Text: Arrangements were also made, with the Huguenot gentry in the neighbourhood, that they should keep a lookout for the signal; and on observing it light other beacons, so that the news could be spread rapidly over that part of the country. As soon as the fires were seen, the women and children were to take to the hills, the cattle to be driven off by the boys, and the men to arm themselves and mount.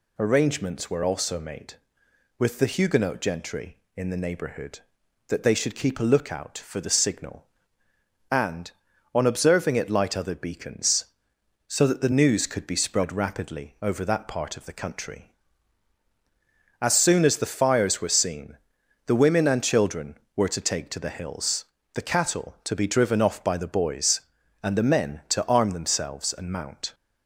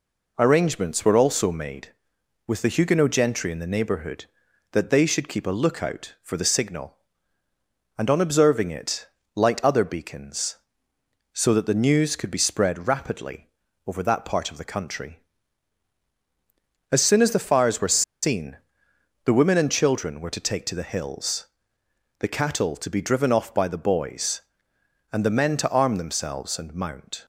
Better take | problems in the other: first | pauses between "it" and "light"; slight; at 9.0 s; 0.30 s long // pauses between "rapidly" and "over"; at 13.4 s; 0.38 s long // pauses between "were" and "seen"; slight; at 18.0 s; 0.19 s long

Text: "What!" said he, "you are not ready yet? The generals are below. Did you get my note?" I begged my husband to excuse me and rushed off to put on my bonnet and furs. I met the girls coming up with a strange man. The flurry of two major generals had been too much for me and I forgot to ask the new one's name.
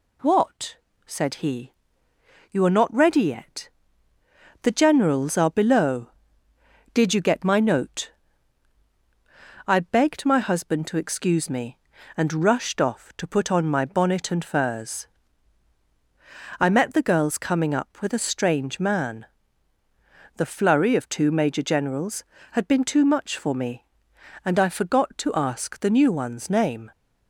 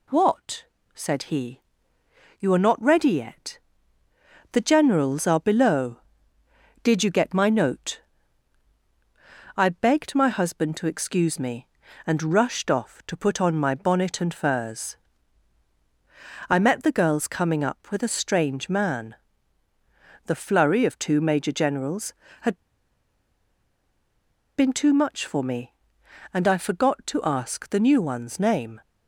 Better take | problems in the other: first | pauses between "had" and "been"; strong; at 22.5 s; 1.9 s long

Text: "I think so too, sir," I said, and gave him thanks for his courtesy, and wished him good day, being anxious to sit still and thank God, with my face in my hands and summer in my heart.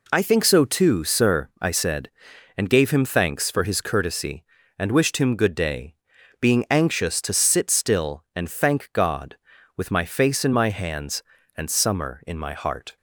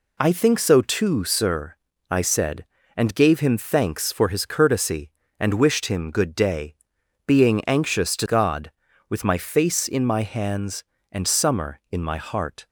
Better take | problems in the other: first | skips "sit still and thank"; at 8.2 s

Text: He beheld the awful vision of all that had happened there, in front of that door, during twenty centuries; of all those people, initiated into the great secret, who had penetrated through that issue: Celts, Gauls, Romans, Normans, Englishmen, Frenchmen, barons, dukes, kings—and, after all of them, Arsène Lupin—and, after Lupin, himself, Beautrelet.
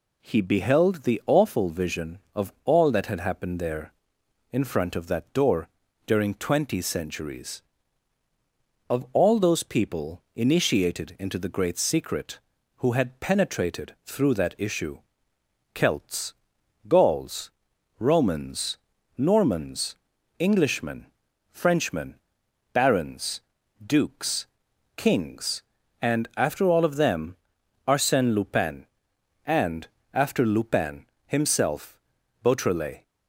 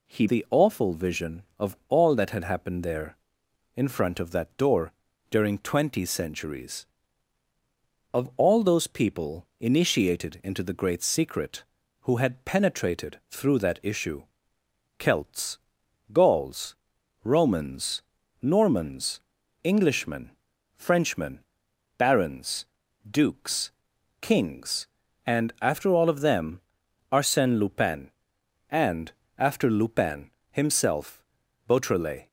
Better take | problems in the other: first | skips "beheld"; at 0.2 s

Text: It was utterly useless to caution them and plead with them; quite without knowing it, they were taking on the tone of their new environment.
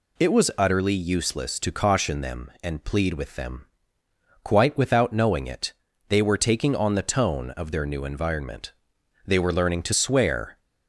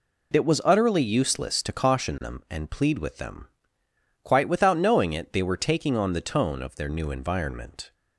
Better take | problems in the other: second | goes on to say "They were learning to swear"; from 9.2 s on; 1.3 s long

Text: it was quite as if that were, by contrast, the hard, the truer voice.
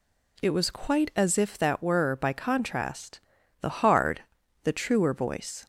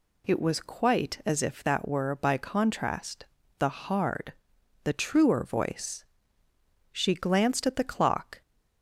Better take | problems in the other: first | goes on to say "She glanced at the clock"; from 6.9 s on; 1.5 s long

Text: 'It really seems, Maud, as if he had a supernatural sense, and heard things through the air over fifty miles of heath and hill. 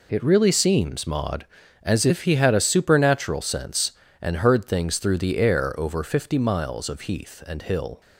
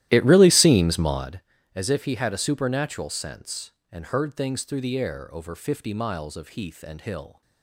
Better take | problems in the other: first | starts louder than the rest; strong; until 1.3 s; 14 dB

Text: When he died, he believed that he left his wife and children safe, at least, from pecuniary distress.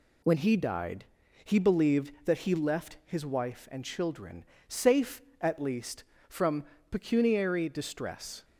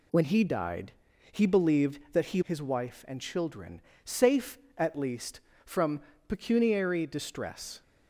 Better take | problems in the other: first | skips "left"; at 2.4 s // pauses between "children" and "safe"; slight; at 3.8 s; 0.22 s long; slight in the first // pauses between "from" and "pecuniary"; slight; at 5.9 s; 0.28 s long; slight in the first

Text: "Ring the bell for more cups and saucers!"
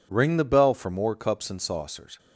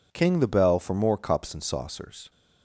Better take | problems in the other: first | says "King" for "Ring"; at 0.1 s

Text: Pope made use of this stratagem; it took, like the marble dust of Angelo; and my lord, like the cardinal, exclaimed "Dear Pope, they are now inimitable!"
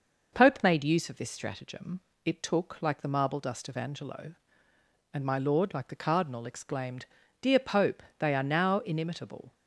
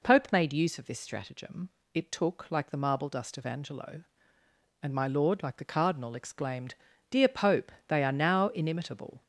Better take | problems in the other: first | gets louder; throughout; 4 dB // pauses between "exclaimed" and "Dear"; slight; at 6.7 s; 0.34 s long; slight in the first

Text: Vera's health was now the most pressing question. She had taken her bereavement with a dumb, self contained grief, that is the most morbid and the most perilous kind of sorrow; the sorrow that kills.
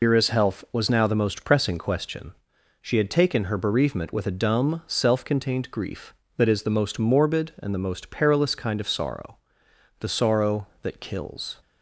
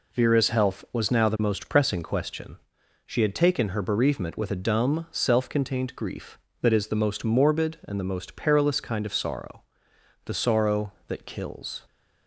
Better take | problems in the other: second | loses the start of "Vera's"; at 0.0 s; 95 ms

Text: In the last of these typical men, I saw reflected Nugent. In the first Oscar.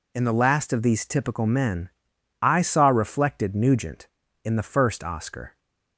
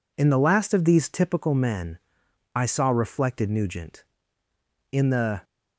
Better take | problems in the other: first | stops before "first Oscar"; at 5.4 s

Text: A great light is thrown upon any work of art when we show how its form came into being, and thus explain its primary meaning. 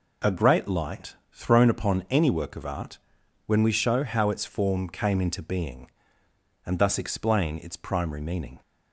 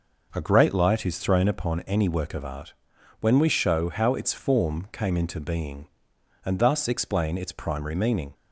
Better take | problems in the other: second | skips "is"; at 1.2 s // pauses between "art" and "when"; noticeable; at 2.9 s; 0.50 s long; noticeable in the second

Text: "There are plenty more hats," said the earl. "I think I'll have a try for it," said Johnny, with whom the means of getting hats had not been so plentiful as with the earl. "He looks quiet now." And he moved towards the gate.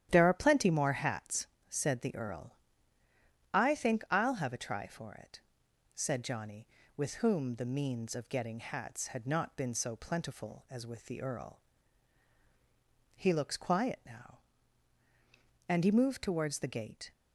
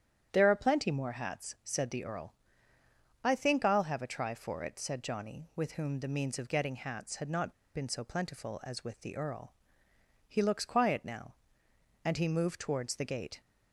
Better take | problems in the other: first | starts louder than the rest; strong; until 1.3 s; 10 dB; strong in the first // pauses between "not" and "been"; slight; at 7.5 s; 0.22 s long

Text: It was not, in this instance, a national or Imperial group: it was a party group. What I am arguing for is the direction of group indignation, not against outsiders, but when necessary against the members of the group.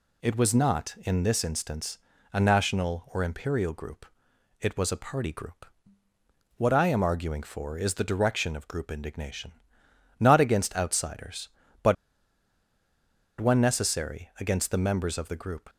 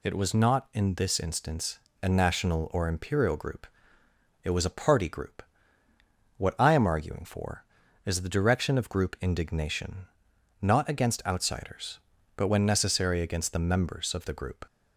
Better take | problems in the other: second | pauses between "but" and "when"; strong; at 11.9 s; 1.4 s long

